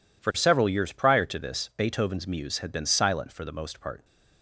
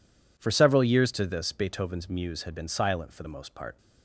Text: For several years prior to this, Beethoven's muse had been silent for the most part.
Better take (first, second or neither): first